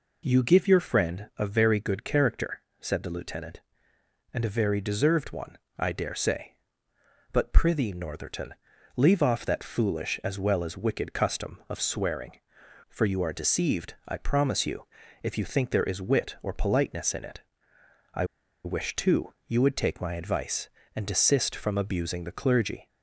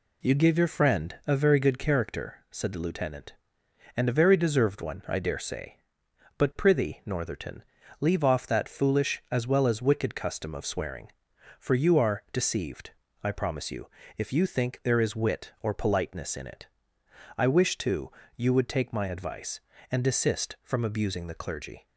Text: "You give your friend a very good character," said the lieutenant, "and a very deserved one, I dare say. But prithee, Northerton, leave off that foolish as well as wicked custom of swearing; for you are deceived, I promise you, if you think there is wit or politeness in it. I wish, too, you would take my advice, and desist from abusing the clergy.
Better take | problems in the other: second | pauses between "I" and "wish"; at 18.2 s; 0.40 s long

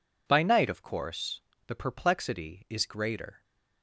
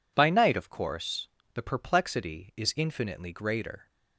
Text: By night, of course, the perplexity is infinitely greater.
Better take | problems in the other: second | skips "infinitely"; at 2.8 s

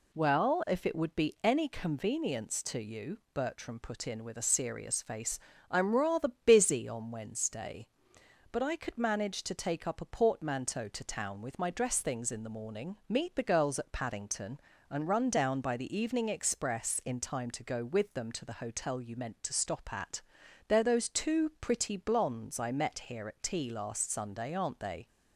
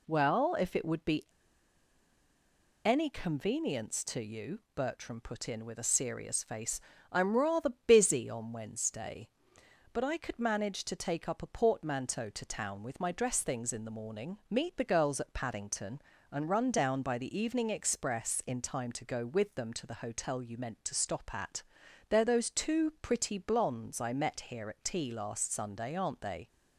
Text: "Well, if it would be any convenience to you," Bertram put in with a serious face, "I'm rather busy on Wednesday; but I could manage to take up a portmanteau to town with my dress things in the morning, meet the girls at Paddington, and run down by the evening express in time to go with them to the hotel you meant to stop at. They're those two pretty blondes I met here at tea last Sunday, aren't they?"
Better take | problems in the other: first | pauses between "be" and "any"; strong; at 1.2 s; 1.5 s long // pauses between "rather" and "busy"; slight; at 7.7 s; 0.16 s long; slight in the first

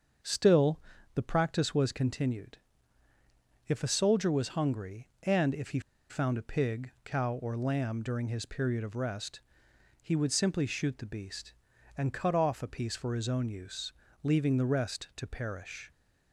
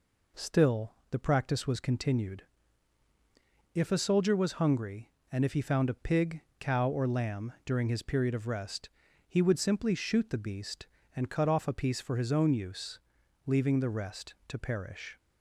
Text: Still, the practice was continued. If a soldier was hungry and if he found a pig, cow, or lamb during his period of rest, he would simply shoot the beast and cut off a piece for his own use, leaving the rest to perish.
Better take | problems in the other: second | starts louder than the rest; until 1.6 s; 7 dB // pauses between "he" and "found"; slight; at 5.7 s; 0.30 s long

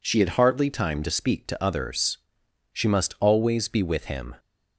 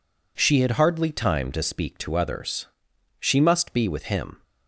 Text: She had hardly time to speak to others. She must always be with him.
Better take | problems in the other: first | skips "always"; at 3.7 s

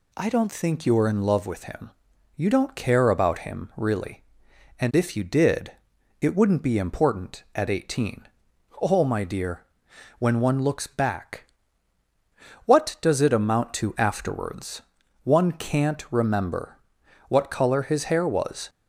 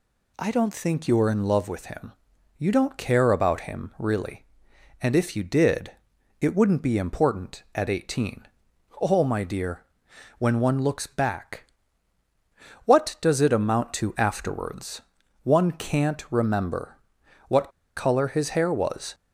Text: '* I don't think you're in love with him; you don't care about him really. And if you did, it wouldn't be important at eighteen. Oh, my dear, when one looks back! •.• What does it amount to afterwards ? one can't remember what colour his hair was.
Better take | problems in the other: first | pauses between "remember" and "what"; noticeable; at 16.9 s; 0.50 s long; noticeable in the first // pauses between "what" and "colour"; slight; at 17.7 s; 0.25 s long

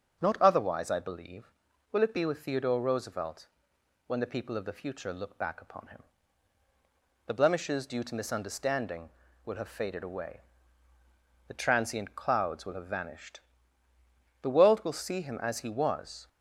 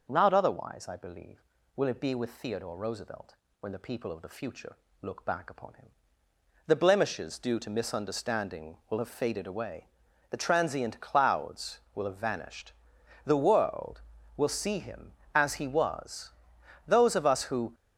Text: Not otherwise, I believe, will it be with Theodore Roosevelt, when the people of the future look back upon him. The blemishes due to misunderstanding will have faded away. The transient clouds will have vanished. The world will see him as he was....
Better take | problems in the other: first | starts louder than the rest; noticeable; until 1.1 s; 6 dB; also in the first // pauses between "future" and "look"; slight; at 4.7 s; 0.26 s long // goes on to say "Those of us who"; noticeable; from 16.8 s on; 0.88 s long

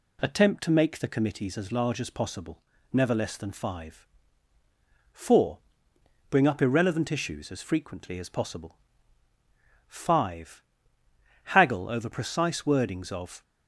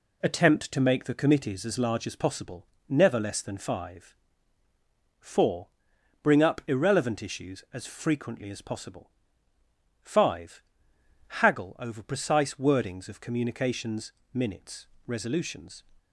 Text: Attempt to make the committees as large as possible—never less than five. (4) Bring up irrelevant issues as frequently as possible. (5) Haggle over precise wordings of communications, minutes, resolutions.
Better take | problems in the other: second | stops before "communications minutes resolutions"; at 13.4 s

